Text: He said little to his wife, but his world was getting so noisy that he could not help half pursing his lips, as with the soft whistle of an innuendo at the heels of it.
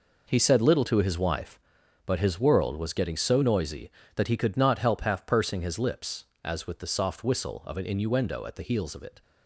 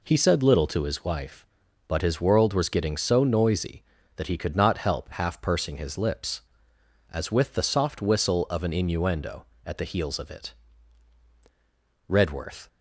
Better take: first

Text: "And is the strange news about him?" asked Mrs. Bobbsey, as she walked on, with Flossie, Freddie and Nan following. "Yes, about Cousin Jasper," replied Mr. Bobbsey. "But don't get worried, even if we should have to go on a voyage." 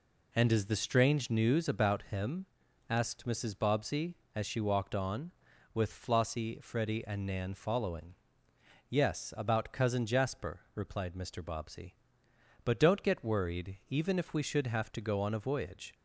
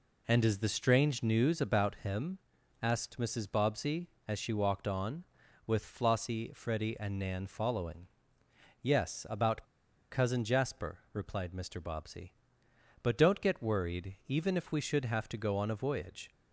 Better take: first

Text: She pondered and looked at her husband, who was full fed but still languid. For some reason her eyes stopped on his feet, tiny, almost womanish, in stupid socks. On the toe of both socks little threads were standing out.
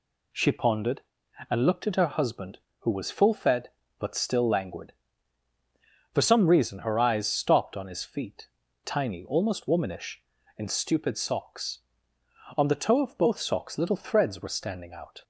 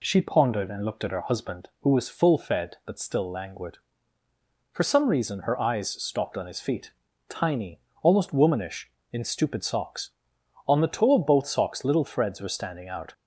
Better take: neither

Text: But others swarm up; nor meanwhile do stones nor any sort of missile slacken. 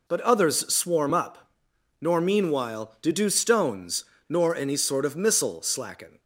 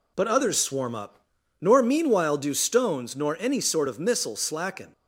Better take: second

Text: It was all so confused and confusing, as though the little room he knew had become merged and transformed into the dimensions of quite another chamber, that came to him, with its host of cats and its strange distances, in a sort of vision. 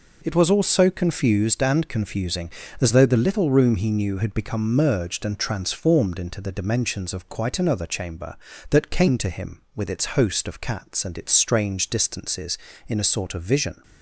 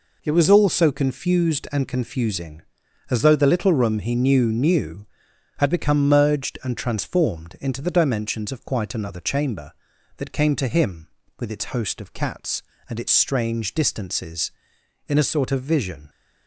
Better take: first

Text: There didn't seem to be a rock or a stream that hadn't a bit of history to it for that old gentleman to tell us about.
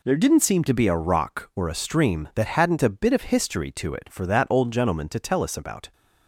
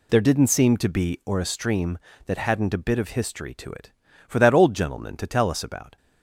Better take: first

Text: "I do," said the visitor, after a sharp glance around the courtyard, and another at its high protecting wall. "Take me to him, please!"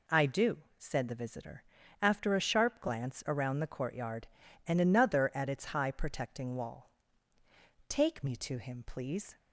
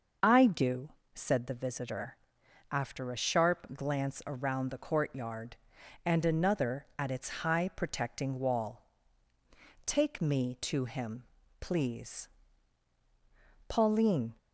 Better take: first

